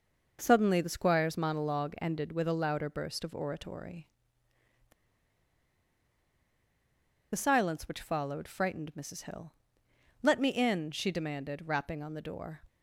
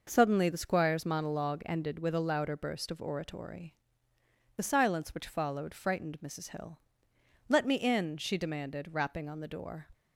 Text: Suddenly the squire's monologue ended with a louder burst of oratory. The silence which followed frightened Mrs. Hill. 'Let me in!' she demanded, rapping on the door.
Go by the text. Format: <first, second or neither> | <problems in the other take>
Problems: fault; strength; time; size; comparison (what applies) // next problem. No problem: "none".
second | pauses between "The" and "silence"; strong; at 4.9 s; 2.4 s long